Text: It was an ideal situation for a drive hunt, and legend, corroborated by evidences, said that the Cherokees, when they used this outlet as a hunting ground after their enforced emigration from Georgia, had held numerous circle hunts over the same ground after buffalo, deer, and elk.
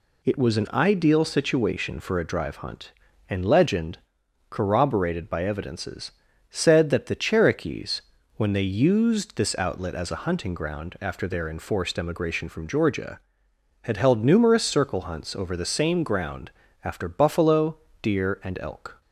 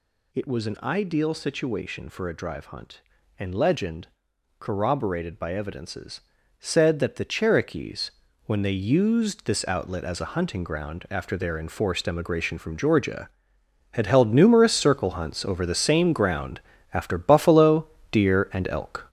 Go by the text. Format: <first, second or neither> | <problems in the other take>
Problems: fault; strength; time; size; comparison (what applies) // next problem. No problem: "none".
first | gets louder; strong; throughout; 7.5 dB // pauses between "ground" and "after"; slight; at 16.5 s; 0.34 s long; slight in the first